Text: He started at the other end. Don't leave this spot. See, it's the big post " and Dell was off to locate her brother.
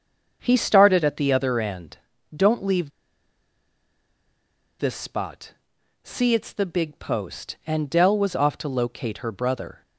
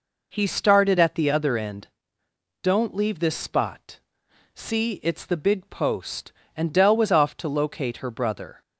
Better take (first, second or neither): second